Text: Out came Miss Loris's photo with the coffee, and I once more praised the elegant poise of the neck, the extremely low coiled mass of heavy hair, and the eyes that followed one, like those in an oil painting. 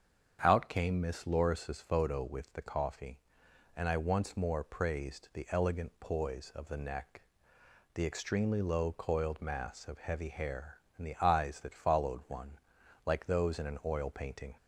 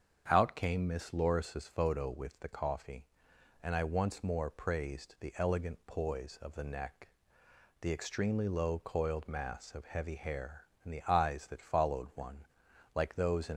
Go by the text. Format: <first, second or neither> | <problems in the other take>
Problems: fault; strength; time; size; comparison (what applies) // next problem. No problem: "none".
first | starts louder than the rest; strong; until 1.2 s; 7.5 dB; strong in the first // stops before "an oil painting"; at 13.5 s